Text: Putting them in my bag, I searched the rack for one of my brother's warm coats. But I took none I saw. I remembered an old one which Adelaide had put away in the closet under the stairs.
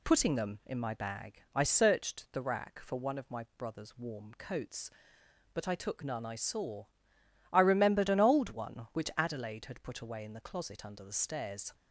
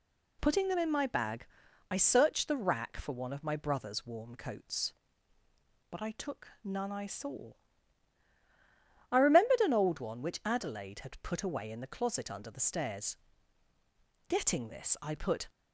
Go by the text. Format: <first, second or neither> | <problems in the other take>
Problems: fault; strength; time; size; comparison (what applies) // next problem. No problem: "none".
first | pauses between "took" and "none"; slight; at 6.4 s; 0.16 s long // goes on to say "Getting this I put"; noticeable; from 14.2 s on; 1.2 s long